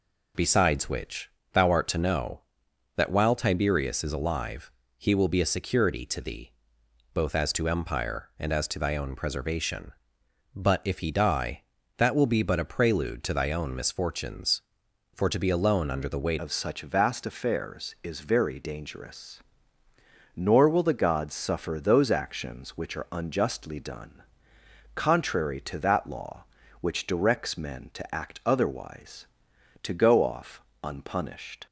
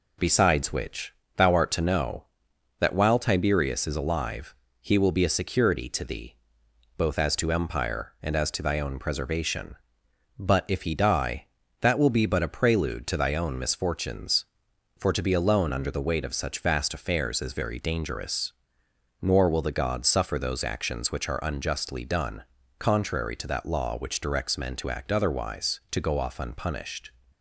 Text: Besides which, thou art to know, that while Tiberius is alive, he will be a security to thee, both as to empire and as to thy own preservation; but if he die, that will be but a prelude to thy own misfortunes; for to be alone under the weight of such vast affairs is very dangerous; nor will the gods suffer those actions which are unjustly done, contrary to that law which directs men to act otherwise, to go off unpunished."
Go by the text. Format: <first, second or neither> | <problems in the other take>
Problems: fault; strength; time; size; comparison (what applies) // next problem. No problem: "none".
second | changes voice at "of"; from 16.3 s on; 15.3 s long // pauses between "off" and "unpunished"; slight; at 30.5 s; 0.24 s long